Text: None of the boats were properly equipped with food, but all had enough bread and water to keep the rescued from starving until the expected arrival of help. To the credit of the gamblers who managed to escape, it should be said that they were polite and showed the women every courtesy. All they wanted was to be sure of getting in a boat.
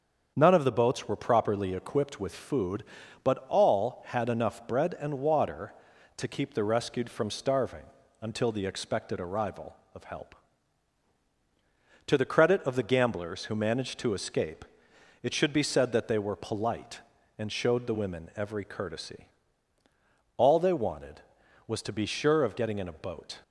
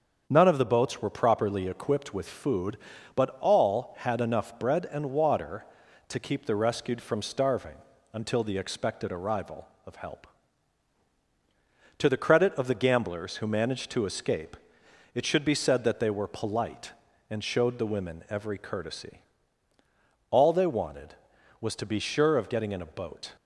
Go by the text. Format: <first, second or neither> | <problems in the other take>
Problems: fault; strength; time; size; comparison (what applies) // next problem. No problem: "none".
neither | starts louder than the rest; the same in both // pauses between "starving" and "until"; slight; the same in both